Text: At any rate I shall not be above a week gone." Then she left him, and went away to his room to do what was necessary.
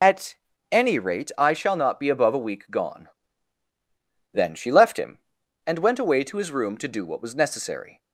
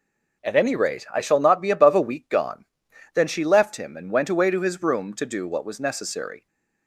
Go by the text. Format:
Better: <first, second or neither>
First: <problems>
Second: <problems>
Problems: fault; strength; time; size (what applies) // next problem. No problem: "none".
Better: second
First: loses the start of "At"; at 0.0 s; 55 ms // pauses between "At" and "any"; slight; at 0.3 s; 0.34 s long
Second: none